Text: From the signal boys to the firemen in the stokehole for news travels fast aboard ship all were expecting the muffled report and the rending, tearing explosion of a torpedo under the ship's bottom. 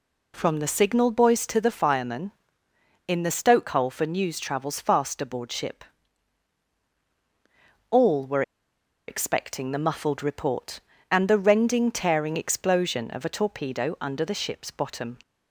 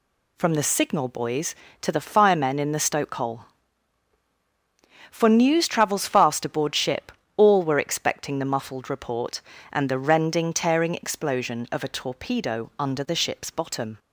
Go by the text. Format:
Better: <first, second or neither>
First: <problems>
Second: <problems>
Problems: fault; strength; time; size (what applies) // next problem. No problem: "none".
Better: second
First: pauses between "ship" and "all"; strong; at 5.8 s; 2.0 s long // pauses between "were" and "expecting"; noticeable; at 8.4 s; 0.65 s long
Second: pauses between "ship" and "all"; slight; at 7.1 s; 0.24 s long